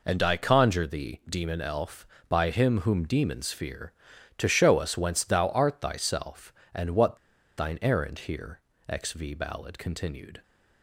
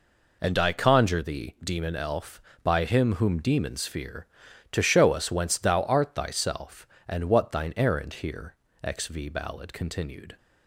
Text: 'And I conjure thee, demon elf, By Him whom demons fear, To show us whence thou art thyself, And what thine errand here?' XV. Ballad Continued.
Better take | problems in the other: second | pauses between "what" and "thine"; at 7.1 s; 0.40 s long

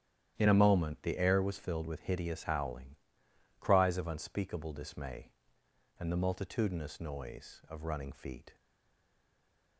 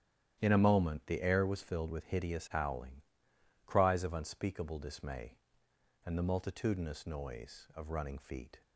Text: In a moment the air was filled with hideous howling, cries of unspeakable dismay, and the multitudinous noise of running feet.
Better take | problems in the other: second | starts louder than the rest; strong; until 1.3 s; 11 dB; strong in the second // stays silent after the last word; noticeable; from 8.5 s on; 1.2 s long

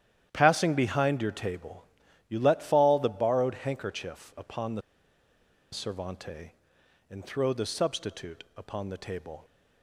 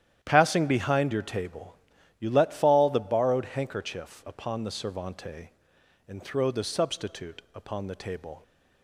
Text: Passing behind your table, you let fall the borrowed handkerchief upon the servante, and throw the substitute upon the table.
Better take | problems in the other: second | starts louder than the rest; strong; until 1.3 s; 11 dB; strong in the second // pauses between "the" and "servante"; noticeable; at 4.8 s; 0.91 s long

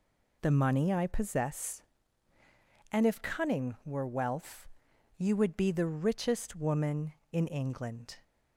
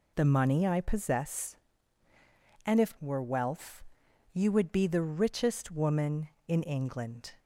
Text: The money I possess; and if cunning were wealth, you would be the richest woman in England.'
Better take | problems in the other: first | skips "cunning"; at 2.9 s

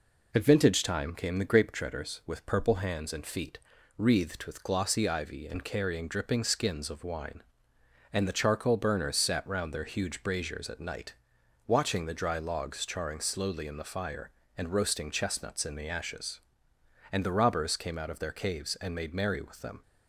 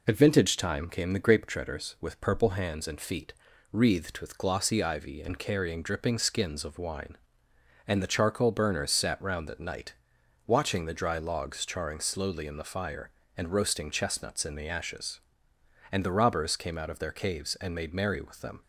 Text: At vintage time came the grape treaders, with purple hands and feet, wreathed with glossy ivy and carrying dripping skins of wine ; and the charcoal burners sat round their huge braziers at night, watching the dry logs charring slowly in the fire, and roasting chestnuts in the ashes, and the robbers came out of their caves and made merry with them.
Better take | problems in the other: first | skips "their huge braziers"; at 9.4 s

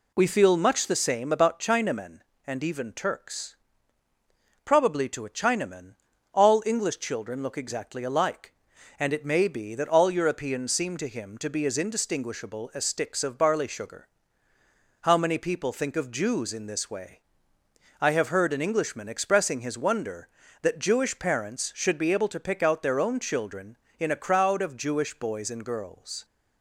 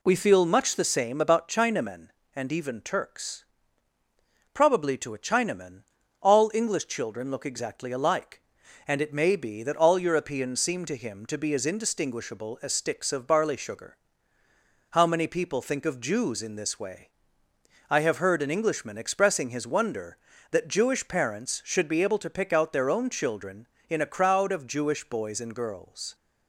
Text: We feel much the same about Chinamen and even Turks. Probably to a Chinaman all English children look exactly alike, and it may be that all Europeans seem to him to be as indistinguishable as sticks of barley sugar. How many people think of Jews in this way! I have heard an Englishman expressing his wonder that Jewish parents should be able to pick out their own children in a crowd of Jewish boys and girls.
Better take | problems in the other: neither | pauses between "Chinaman" and "all"; the same in both

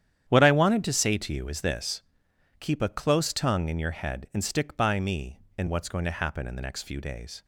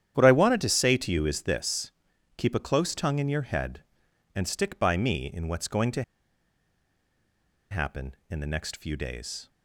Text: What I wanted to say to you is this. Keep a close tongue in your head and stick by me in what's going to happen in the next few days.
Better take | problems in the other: first | starts louder than the rest; strong; until 1.1 s; 10 dB; strong in the first // pauses between "to" and "happen"; strong; at 6.0 s; 1.6 s long

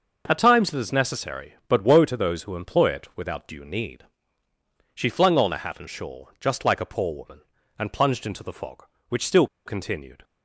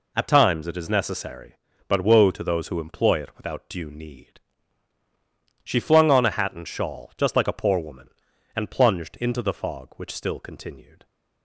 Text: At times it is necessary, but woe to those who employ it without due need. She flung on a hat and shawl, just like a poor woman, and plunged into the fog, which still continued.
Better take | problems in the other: second | pauses between "still" and "continued"; slight; at 9.4 s; 0.19 s long

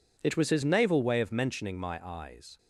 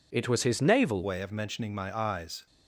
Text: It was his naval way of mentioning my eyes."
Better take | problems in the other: first | changes voice at "way"; from 1.0 s on; 1.4 s long

